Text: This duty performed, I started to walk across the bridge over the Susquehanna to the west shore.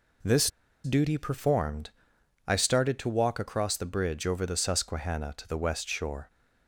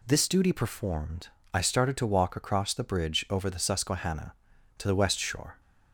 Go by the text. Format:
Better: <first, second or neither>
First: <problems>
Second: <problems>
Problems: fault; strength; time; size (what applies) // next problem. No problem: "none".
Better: second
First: pauses between "This" and "duty"; slight; at 0.4 s; 0.34 s long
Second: none